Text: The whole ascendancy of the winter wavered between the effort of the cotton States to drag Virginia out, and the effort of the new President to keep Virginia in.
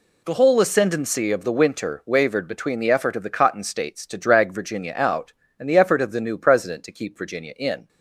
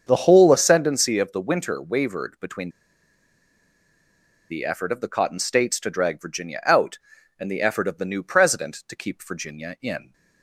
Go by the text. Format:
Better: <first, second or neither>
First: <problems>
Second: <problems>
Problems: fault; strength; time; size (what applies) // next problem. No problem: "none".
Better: first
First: none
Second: starts louder than the rest; until 1.0 s; 7 dB // pauses between "between" and "the"; strong; at 2.6 s; 1.8 s long